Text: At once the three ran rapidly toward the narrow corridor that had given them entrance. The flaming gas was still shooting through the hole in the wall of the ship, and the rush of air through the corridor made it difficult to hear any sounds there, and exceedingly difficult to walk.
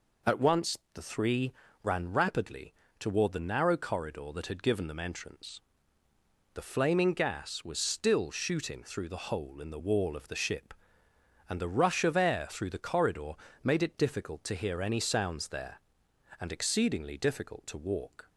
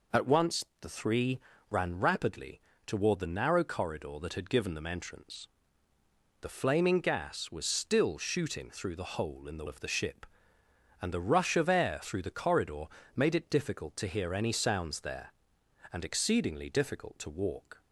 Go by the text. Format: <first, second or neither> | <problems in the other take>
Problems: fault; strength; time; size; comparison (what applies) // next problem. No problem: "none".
first | pauses between "once" and "the"; slight; at 0.6 s; 0.18 s long; slight in the first // pauses between "three" and "ran"; slight; at 1.3 s; 0.30 s long; slight in the first // pauses between "rapidly" and "toward"; slight; at 2.5 s; 0.26 s long; slight in the first // skips "wall"; at 9.6 s // pauses between "corridor" and "made"; slight; at 12.8 s; 0.30 s long; slight in the first